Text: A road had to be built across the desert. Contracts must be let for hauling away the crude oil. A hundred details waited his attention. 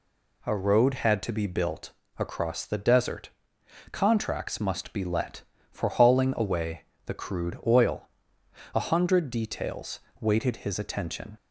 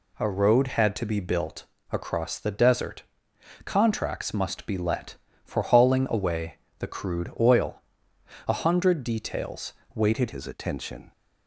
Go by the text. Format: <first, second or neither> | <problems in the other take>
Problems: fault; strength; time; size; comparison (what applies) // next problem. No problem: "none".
first | pauses between "built" and "across"; slight; at 1.6 s; 0.26 s long; slight in the first // pauses between "away" and "the"; slight; at 6.5 s; 0.20 s long; slight in the first // pauses between "details" and "waited"; slight; at 9.7 s; 0.22 s long; slight in the first // changes voice at "his"; from 10.3 s on; 0.8 s long